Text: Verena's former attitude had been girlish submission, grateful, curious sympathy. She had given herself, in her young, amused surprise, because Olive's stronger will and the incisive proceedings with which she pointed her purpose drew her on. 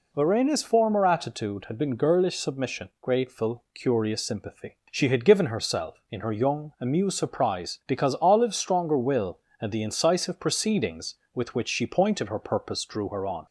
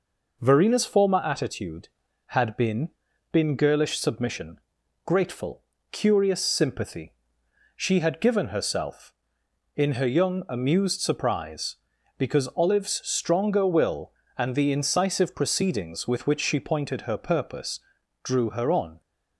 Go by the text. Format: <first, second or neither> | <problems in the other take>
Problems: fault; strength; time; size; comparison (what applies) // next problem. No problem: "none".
first | says "been" twice; at 3.3 s // pauses between "purpose" and "drew"; at 17.8 s; 0.42 s long